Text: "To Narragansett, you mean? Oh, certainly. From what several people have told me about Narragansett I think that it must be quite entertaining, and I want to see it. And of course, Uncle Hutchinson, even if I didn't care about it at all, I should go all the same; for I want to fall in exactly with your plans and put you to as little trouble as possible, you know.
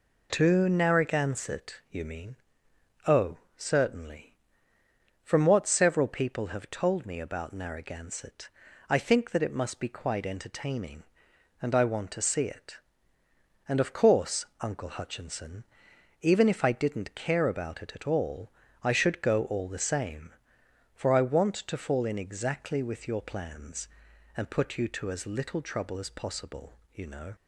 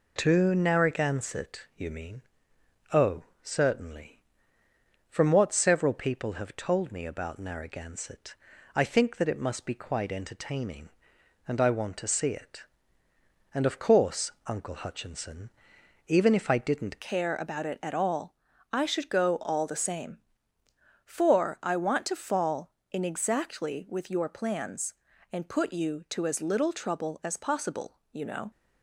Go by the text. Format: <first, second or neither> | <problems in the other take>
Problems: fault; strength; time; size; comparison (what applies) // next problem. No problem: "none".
first | pauses between "Narragansett" and "I"; at 8.3 s; 0.40 s long; also in the first // changes voice at "care"; from 17.0 s on; 11.5 s long